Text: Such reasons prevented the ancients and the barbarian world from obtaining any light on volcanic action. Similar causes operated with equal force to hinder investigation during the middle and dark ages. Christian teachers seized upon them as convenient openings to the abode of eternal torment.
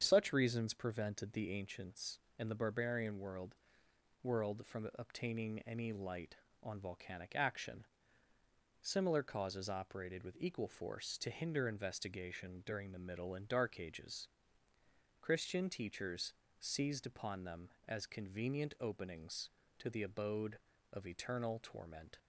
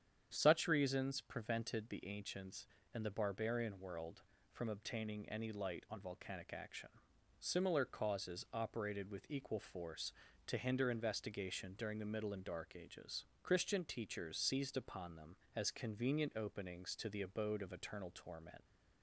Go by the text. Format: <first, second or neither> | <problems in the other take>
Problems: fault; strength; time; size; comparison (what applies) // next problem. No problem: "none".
second | starts louder than the rest; strong; until 1.0 s; 7.5 dB; strong in the second // says "world" twice; at 4.2 s // pauses between "teachers" and "seized"; slight; at 16.3 s; 0.26 s long